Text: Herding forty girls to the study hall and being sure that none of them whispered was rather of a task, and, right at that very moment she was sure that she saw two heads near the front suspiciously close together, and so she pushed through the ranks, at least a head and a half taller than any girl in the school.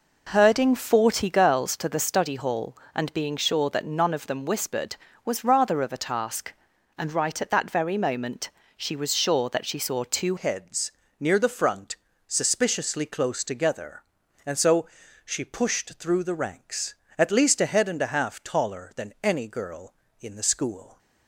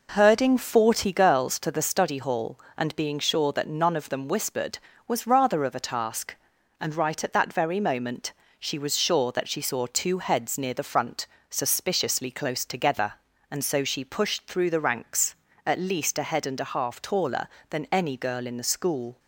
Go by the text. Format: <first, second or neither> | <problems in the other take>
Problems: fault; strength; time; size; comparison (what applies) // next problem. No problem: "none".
second | pauses between "moment" and "she"; slight; at 8.4 s; 0.26 s long; slight in the second // changes voice at "heads"; from 10.3 s on; 10.6 s long // pauses between "heads" and "near"; slight; at 10.9 s; 0.26 s long // pauses between "front" and "suspiciously"; slight; at 11.9 s; 0.32 s long; slight in the second // pauses between "so" and "she"; at 14.8 s; 0.38 s long